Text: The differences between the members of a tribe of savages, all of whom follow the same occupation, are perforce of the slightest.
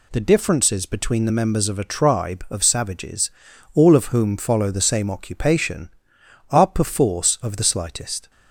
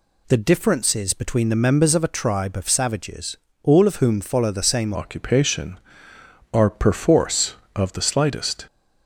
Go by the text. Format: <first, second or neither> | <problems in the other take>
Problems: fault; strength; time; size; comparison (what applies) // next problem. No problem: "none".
first | changes voice at "occupation"; from 4.9 s on; 3.7 s long